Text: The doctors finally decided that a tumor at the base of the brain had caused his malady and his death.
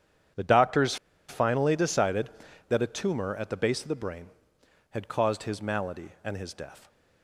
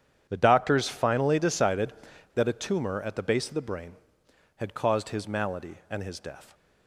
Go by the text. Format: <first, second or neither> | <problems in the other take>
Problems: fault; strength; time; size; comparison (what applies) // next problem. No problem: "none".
second | starts louder than the rest; strong; until 1.6 s; 9 dB; strong in the second // pauses between "doctors" and "finally"; slight; at 0.9 s; 0.32 s long